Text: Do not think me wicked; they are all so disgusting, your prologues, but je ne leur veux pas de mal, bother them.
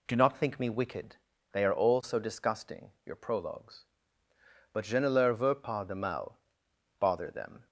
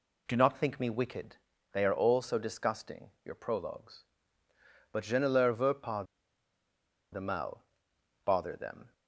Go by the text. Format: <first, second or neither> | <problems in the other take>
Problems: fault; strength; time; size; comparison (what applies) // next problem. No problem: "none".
first | pauses between "pas" and "de"; at 6.0 s; 1.0 s long